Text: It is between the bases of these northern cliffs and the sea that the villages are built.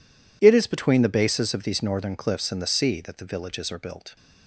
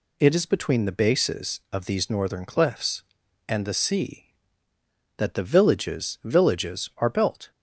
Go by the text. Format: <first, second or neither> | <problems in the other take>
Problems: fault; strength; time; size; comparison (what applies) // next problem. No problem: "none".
first | says "villages" twice; at 6.2 s